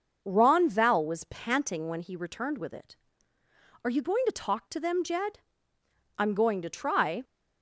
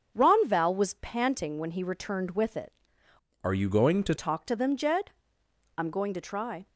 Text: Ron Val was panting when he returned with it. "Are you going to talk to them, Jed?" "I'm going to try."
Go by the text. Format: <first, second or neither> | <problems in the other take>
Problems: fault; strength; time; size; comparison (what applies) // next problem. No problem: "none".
first | starts louder than the rest; until 1.1 s; 7 dB // changes voice from "Are" to "to"; from 3.4 to 4.1 s; 0.7 s long